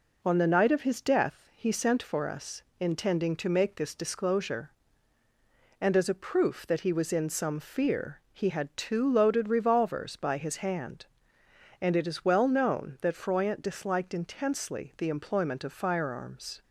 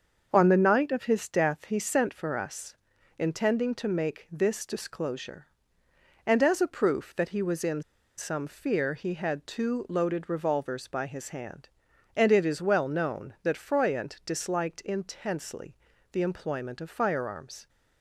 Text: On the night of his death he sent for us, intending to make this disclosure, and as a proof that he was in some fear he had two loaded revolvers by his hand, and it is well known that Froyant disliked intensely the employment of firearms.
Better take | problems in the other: first | starts louder than the rest; until 1.3 s; 6.5 dB // pauses between "in" and "some"; slight; at 7.8 s; 0.35 s long // pauses between "intensely" and "the"; slight; at 15.7 s; 0.34 s long

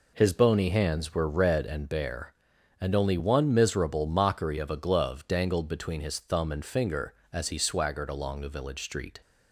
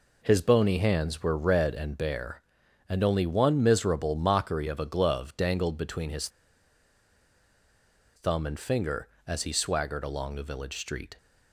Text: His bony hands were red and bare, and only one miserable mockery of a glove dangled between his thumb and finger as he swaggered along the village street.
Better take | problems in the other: first | pauses between "his" and "thumb"; strong; at 6.2 s; 1.8 s long

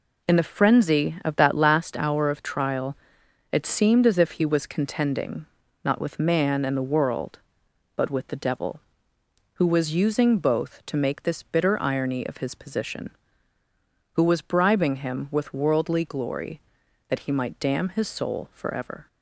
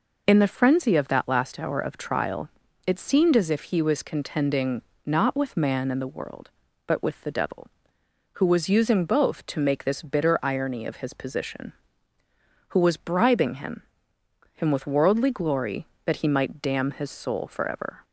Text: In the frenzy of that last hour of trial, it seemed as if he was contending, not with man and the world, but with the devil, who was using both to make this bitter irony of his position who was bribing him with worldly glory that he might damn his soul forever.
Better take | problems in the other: first | says "him" twice; at 14.5 s

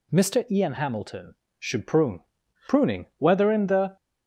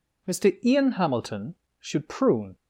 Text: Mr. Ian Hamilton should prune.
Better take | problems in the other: second | goes on to say "Pruning whether in the"; noticeable; from 2.6 s on; 1.2 s long

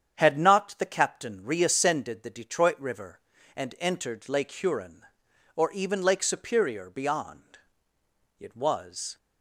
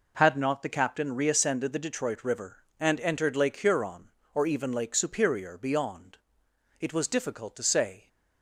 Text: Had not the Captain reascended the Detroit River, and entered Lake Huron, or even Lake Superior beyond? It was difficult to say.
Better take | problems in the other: second | starts louder than the rest; strong; until 1.1 s; 8.5 dB // stops before "difficult to say"; at 9.1 s

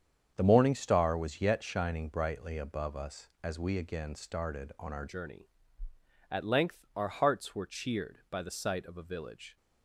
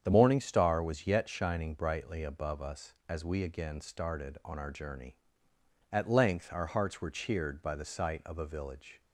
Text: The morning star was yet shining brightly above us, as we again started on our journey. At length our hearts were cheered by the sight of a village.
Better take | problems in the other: second | starts louder than the rest; strong; until 1.3 s; 8 dB; strong in the second // changes voice at "journey"; from 5.0 s on; 4.5 s long

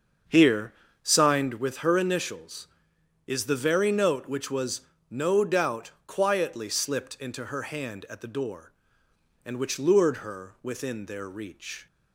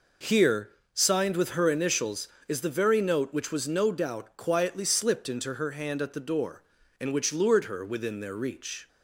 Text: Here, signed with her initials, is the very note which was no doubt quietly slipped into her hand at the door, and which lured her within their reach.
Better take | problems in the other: second | starts louder than the rest; until 1.6 s; 7 dB // pauses between "was" and "no"; slight; at 4.8 s; 0.28 s long // pauses between "doubt" and "quietly"; slight; at 5.9 s; 0.16 s long

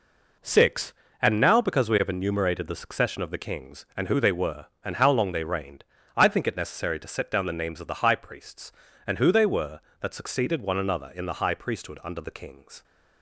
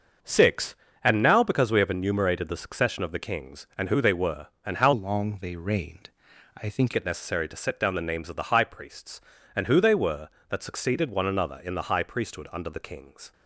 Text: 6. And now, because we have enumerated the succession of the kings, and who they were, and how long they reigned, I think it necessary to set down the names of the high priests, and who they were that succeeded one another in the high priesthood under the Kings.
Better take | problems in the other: first | starts louder than the rest; until 1.5 s; 6.5 dB // changes voice from "long" to "think"; from 4.9 to 6.9 s; 2.0 s long

